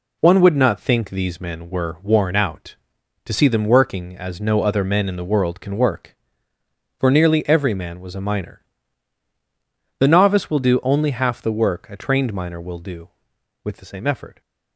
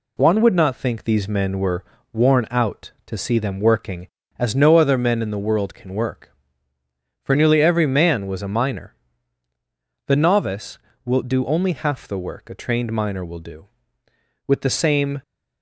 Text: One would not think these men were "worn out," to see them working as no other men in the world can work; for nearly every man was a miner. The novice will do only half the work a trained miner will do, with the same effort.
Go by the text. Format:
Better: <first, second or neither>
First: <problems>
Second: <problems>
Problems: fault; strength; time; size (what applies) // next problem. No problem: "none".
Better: first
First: none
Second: pauses between "were" and "worn"; slight; at 1.8 s; 0.28 s long // stops before "effort"; at 15.2 s